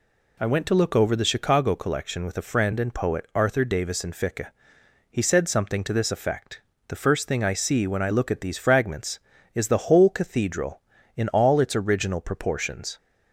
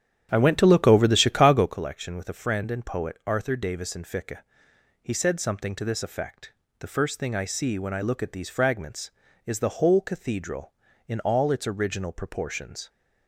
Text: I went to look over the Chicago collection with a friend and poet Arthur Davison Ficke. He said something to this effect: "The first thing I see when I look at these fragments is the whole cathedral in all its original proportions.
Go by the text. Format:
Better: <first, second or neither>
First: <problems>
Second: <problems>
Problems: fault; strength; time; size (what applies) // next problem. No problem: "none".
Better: first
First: none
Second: starts louder than the rest; strong; until 1.8 s; 9.5 dB